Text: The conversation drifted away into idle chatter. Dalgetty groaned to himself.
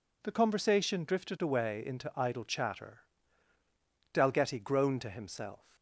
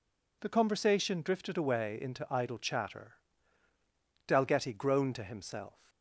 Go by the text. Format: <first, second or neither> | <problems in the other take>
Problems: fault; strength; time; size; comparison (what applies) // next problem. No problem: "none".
neither | none